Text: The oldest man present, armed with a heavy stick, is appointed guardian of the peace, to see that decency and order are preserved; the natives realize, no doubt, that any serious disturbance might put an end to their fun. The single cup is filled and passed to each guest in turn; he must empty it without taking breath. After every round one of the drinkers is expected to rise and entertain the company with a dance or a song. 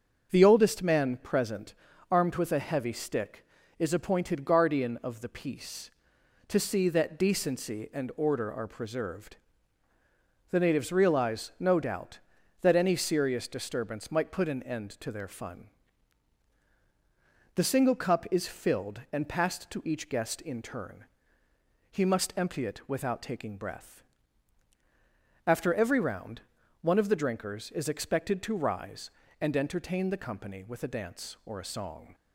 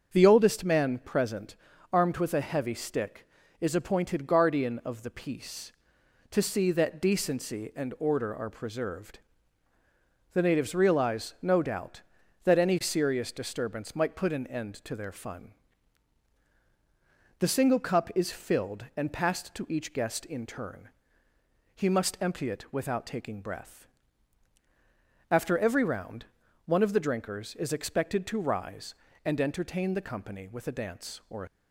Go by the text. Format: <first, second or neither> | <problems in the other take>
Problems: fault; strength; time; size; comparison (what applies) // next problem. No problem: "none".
first | starts louder than the rest; until 1.1 s; 6.5 dB; also in the first // pauses between "round" and "one"; at 26.2 s; 0.40 s long; also in the first // stops before "song"; at 31.4 s